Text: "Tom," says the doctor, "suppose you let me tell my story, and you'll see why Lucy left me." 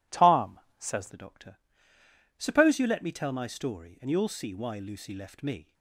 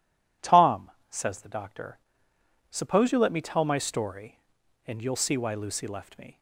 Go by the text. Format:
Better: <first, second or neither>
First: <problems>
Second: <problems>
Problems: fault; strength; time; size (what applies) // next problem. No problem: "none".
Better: second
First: changes voice at "the"; from 1.1 s on; 4.6 s long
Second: none